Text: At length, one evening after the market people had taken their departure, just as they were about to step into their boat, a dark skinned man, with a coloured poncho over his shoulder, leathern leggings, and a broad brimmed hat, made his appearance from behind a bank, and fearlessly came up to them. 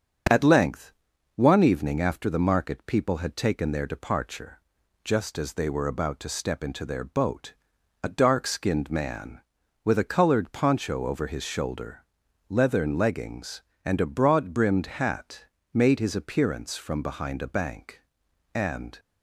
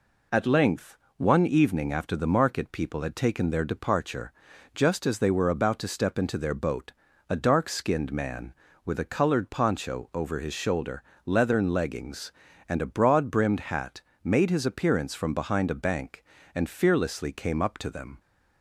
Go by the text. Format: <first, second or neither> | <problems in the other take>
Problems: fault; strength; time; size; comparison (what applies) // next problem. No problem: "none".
second | starts louder than the rest; strong; until 1.7 s; 8 dB // stops before "fearlessly came up to them"; at 18.9 s